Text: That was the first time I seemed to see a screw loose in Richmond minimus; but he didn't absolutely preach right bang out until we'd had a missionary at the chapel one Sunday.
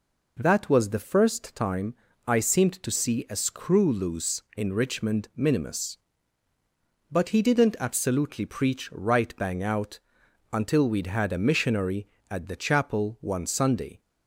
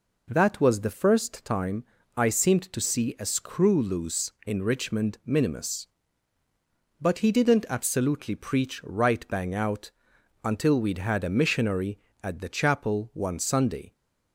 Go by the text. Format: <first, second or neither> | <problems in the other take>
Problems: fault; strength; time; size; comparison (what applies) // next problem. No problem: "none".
neither | pauses between "time" and "I"; slight; the same in both // pauses between "out" and "until"; noticeable; the same in both